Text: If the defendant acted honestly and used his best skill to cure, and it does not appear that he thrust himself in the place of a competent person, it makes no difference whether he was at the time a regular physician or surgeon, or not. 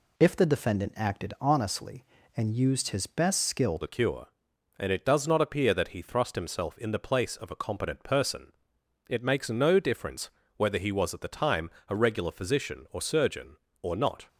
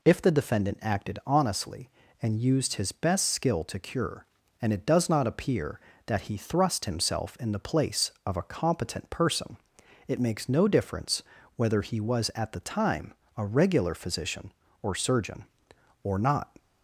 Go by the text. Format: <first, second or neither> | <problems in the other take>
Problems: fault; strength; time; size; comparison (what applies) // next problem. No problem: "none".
second | changes voice at "to"; from 3.8 s on; 10.4 s long // pauses between "difference" and "whether"; slight; at 10.2 s; 0.28 s long; slight in the second // pauses between "time" and "a"; slight; at 11.6 s; 0.18 s long; slight in the second